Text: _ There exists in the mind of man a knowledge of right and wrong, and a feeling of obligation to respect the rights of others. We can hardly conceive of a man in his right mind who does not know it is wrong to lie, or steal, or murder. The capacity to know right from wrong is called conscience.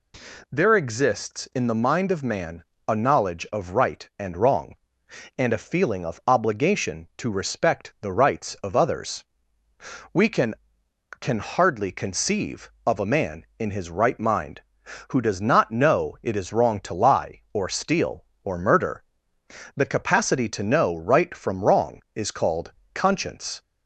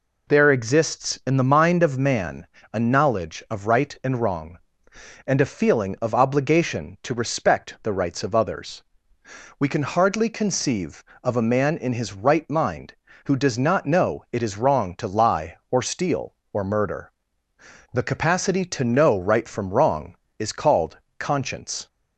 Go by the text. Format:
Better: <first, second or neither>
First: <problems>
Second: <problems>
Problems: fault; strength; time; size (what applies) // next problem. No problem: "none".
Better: second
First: pauses between "man" and "a"; slight; at 2.6 s; 0.24 s long // says "can" twice; at 11.1 s // pauses between "called" and "conscience"; slight; at 22.7 s; 0.22 s long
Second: pauses between "man" and "a"; slight; at 2.4 s; 0.26 s long // pauses between "called" and "conscience"; slight; at 20.9 s; 0.22 s long